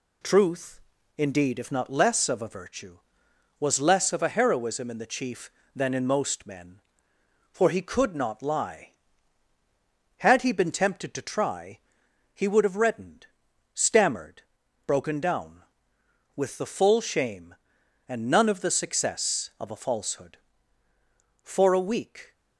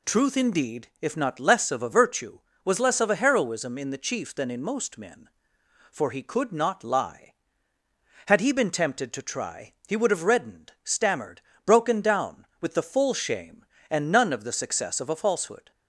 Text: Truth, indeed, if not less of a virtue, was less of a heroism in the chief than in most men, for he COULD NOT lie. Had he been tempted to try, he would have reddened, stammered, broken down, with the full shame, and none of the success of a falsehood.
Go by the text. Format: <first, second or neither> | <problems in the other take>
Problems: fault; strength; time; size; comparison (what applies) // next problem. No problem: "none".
second | goes on to say "For a week"; noticeable; from 21.4 s on; 0.90 s long